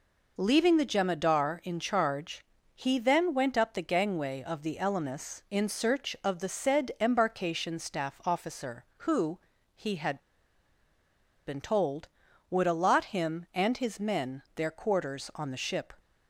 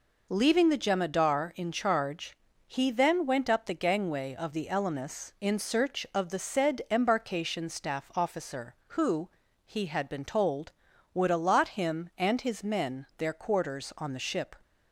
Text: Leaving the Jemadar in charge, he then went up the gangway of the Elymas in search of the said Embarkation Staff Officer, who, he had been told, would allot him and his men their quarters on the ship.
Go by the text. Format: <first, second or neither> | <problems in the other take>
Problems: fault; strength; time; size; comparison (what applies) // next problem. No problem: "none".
second | pauses between "had" and "been"; strong; at 10.1 s; 1.2 s long